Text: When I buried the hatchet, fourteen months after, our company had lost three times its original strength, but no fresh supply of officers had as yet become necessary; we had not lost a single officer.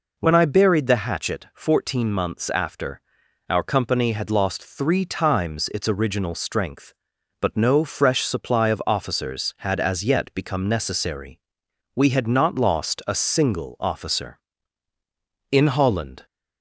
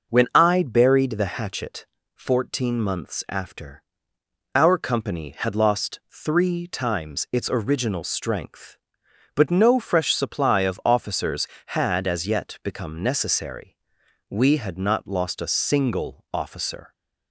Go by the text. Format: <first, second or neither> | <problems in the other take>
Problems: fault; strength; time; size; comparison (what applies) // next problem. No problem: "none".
second | goes on to say "In Holland"; noticeable; from 15.5 s on; 0.74 s long